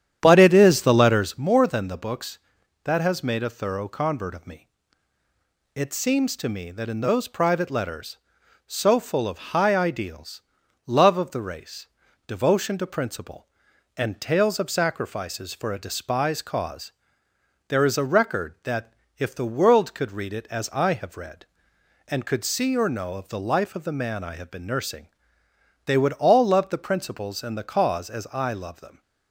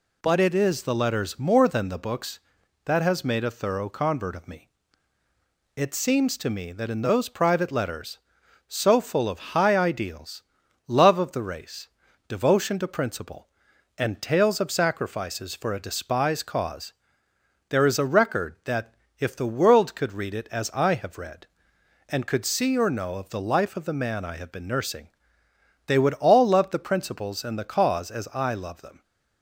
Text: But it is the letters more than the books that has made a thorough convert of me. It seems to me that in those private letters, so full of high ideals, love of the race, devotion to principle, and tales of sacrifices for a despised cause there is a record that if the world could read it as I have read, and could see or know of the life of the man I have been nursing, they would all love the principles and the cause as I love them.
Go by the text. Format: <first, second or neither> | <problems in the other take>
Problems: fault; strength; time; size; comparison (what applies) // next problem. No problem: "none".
second | starts louder than the rest; strong; until 1.4 s; 9.5 dB // pauses between "cause" and "there"; noticeable; at 16.9 s; 0.76 s long; noticeable in the second // pauses between "that" and "if"; slight; at 18.9 s; 0.22 s long; slight in the second